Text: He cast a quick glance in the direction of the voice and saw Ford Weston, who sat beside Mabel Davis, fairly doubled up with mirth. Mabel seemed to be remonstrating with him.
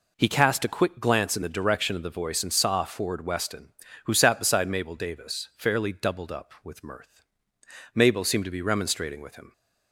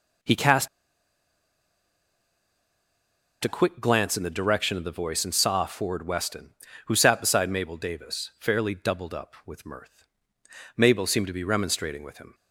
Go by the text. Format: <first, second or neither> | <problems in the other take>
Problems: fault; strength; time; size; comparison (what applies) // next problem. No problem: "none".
first | pauses between "cast" and "a"; strong; at 0.6 s; 2.7 s long